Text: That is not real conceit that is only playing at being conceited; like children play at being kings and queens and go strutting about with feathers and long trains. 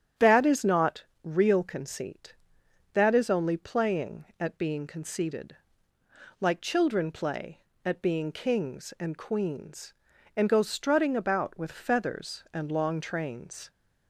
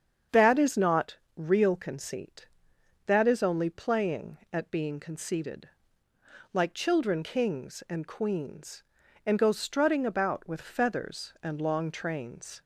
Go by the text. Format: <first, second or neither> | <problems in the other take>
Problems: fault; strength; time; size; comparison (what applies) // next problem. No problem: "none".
first | starts louder than the rest; strong; until 1.5 s; 7.5 dB; strong in the first // pauses between "not" and "real"; slight; at 1.1 s; 0.18 s long; slight in the first // skips "play at being"; at 7.2 s